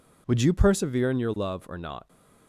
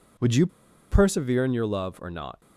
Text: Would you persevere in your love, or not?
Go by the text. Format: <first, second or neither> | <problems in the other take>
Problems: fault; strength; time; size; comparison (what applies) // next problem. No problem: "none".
first | pauses between "you" and "persevere"; at 0.4 s; 0.44 s long